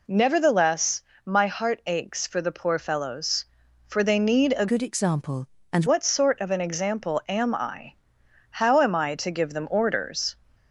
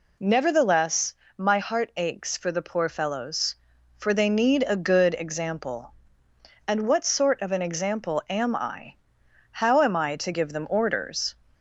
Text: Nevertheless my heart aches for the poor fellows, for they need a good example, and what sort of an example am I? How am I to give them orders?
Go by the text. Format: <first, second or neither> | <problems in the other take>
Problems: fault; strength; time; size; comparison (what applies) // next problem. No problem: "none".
second | pauses between "Nevertheless" and "my"; slight; at 1.0 s; 0.24 s long; slight in the second // changes voice from "good" to "and"; from 4.6 to 5.8 s; 1.2 s long